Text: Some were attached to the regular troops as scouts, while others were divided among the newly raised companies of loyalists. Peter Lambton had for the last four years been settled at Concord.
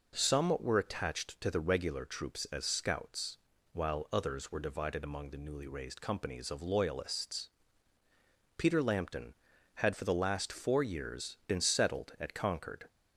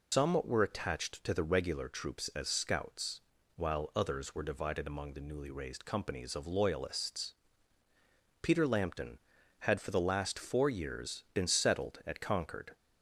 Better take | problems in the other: first | loses the start of "Some"; at 0.1 s; 145 ms

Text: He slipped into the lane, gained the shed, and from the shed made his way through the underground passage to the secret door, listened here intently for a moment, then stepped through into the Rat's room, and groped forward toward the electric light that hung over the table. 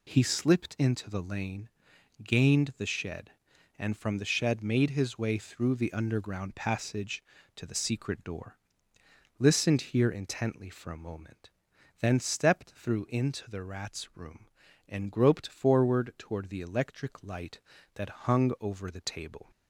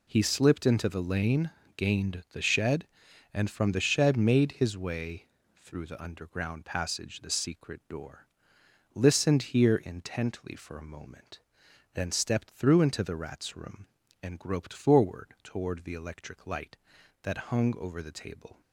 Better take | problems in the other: first | pauses between "way" and "through"; slight; at 5.2 s; 0.36 s long // skips "to"; at 7.1 s

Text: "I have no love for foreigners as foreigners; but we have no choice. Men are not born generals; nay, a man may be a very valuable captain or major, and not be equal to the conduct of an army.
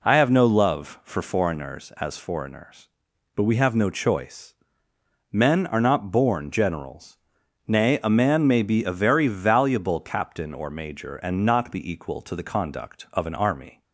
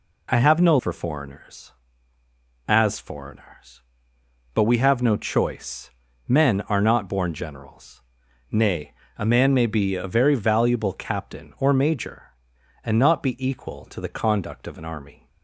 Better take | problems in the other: first | skips "love"; at 0.7 s

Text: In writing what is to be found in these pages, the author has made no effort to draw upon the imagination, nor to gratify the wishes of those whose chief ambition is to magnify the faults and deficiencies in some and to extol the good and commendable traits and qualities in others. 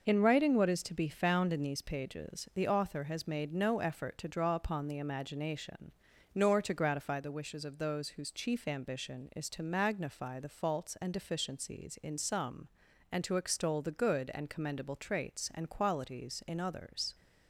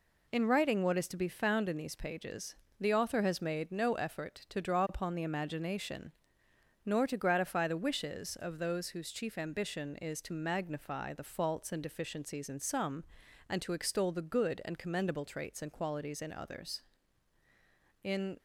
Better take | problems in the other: first | goes on to say "In"; slight; from 18.0 s on; 0.34 s long

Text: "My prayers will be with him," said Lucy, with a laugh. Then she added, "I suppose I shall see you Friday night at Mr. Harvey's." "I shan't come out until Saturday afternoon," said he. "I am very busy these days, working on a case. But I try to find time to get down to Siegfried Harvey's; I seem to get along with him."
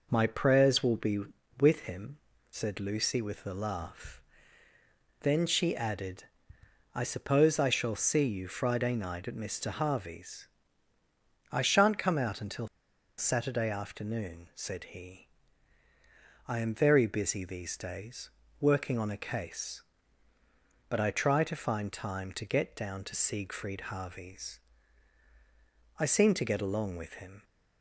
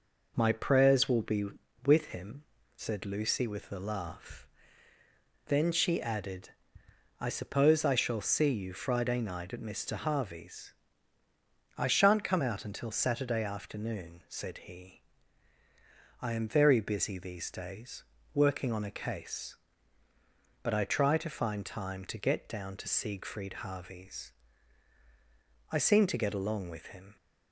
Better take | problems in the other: second | pauses between "until" and "Saturday"; noticeable; at 12.6 s; 0.52 s long

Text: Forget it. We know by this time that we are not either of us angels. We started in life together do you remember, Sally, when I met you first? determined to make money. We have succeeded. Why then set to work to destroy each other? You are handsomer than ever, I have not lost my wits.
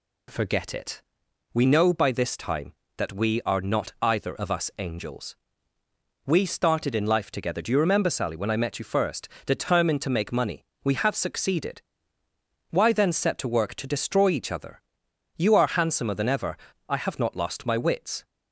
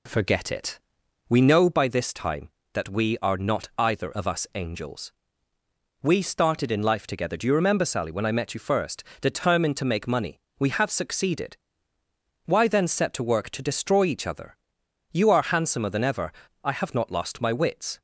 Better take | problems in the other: first | starts louder than the rest; slight; until 1.8 s; 3 dB

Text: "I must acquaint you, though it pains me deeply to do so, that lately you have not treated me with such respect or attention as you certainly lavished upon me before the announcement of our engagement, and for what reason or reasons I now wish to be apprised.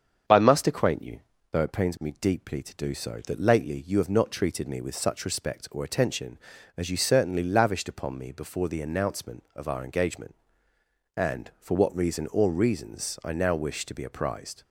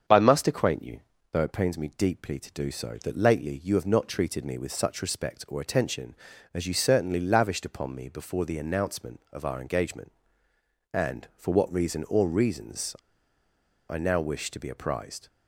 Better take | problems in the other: first | starts louder than the rest; strong; until 1.4 s; 7.5 dB; strong in the first // pauses between "reasons" and "I"; noticeable; at 12.9 s; 0.94 s long

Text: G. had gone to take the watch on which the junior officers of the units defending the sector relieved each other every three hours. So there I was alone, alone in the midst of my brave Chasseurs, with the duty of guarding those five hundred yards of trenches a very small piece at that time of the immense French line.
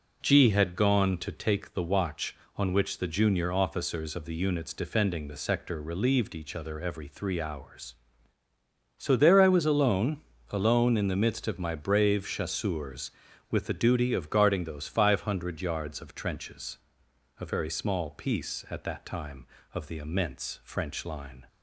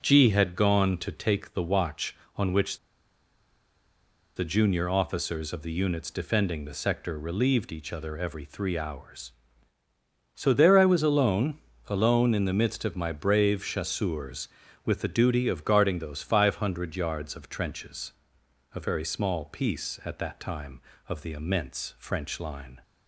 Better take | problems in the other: first | pauses between "which" and "the"; strong; at 2.7 s; 1.5 s long // pauses between "trenches" and "a"; noticeable; at 18.1 s; 0.62 s long; noticeable in the first

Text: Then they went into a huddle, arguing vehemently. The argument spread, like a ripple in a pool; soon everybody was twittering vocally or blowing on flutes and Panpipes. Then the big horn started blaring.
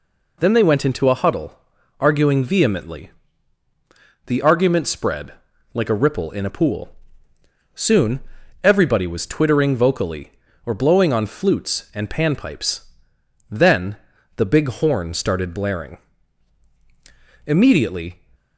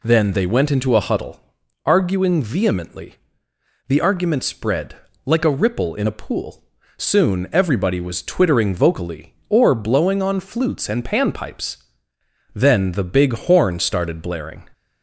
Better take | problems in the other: second | pauses between "soon" and "everybody"; at 8.2 s; 0.42 s long // pauses between "Then" and "the"; at 13.9 s; 0.40 s long // goes on to say "Immediately"; noticeable; from 17.4 s on; 0.78 s long

